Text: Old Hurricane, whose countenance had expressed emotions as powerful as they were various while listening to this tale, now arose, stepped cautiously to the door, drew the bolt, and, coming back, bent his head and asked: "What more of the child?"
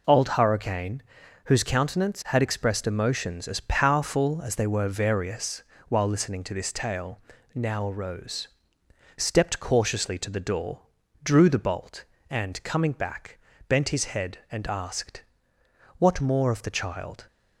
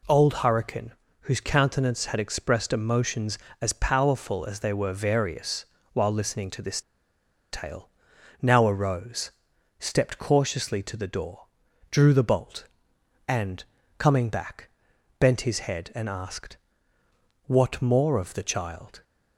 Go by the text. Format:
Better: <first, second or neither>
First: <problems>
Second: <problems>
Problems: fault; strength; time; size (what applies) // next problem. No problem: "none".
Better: first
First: pauses between "various" and "while"; slight; at 5.6 s; 0.24 s long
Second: pauses between "various" and "while"; slight; at 5.6 s; 0.30 s long // pauses between "this" and "tale"; noticeable; at 6.8 s; 0.70 s long